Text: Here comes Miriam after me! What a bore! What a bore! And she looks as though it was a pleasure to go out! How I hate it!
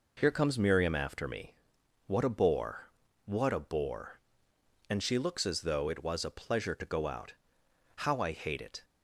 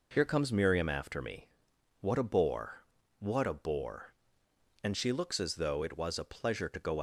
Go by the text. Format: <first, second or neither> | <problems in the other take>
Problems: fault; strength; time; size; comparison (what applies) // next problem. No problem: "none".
first | stops before "out How I hate it"; at 6.9 s